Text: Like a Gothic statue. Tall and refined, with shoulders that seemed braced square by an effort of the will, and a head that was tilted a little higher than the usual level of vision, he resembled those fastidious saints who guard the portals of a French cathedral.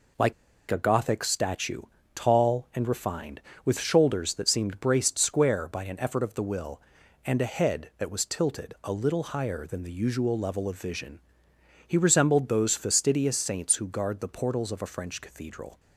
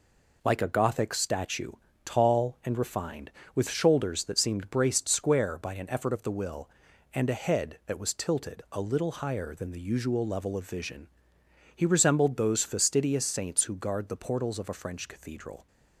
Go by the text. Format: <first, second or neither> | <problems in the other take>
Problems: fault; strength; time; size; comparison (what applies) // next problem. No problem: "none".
second | pauses between "Like" and "a"; at 0.3 s; 0.38 s long